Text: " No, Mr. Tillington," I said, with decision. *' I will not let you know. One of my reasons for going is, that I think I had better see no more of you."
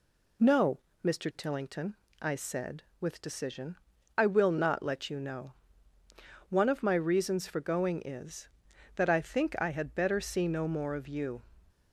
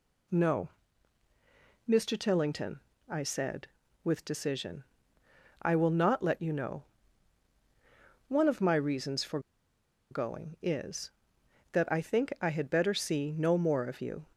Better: first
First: none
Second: pauses between "for" and "going"; noticeable; at 9.3 s; 0.71 s long

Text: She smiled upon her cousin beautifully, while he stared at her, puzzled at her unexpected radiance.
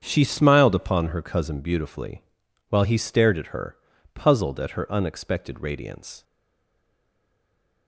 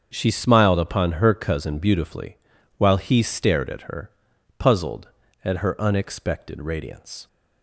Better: second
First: starts louder than the rest; strong; until 1.0 s; 7.5 dB // stays silent after the last word; noticeable; from 6.2 s on; 1.6 s long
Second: starts louder than the rest; until 1.1 s; 7 dB

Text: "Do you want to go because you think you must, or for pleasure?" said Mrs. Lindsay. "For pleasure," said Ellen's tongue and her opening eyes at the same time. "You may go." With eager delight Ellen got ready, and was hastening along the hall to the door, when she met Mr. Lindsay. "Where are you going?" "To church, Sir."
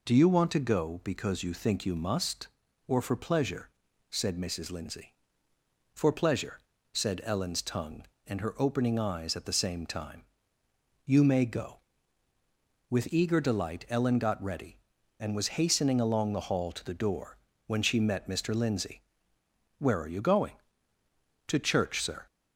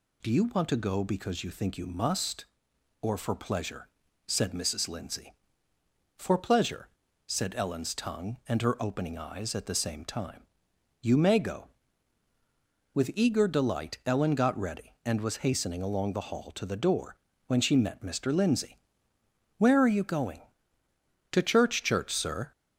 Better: first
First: none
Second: says "church" twice; at 21.8 s

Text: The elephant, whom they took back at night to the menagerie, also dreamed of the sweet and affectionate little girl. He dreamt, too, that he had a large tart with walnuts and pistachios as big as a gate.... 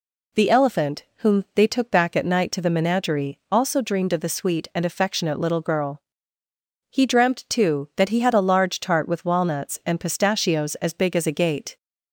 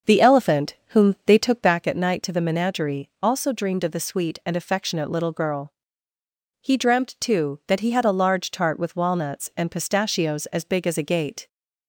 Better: first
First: none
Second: starts louder than the rest; noticeable; until 1.8 s; 6 dB

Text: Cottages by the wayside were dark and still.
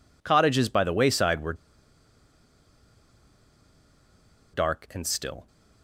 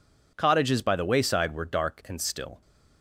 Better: second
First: pauses between "were" and "dark"; strong; at 1.5 s; 2.9 s long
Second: none

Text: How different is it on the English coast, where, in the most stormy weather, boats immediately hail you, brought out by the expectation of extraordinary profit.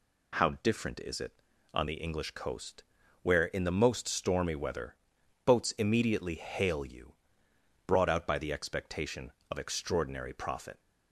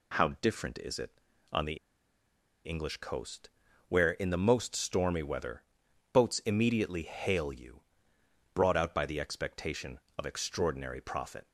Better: first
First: none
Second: pauses between "the" and "English"; noticeable; at 1.7 s; 0.88 s long

